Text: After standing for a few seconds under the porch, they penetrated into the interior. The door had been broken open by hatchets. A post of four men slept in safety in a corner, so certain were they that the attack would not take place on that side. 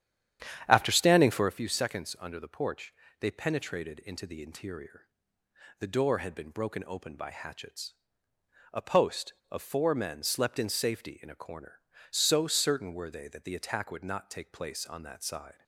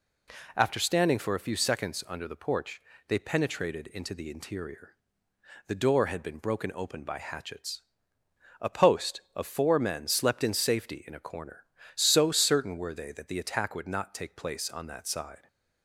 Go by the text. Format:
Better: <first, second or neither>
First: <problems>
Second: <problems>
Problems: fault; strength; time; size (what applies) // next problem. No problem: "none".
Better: second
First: starts louder than the rest; strong; until 1.6 s; 9.5 dB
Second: none